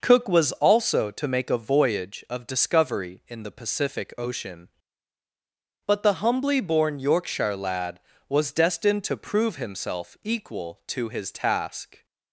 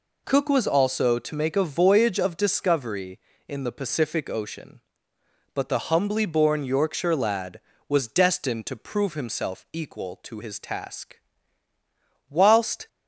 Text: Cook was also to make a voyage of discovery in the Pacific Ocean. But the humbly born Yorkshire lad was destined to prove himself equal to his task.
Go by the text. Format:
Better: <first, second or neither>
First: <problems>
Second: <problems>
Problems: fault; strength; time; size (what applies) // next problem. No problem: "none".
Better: first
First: none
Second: goes on to say "Whilst"; from 12.2 s on; 0.58 s long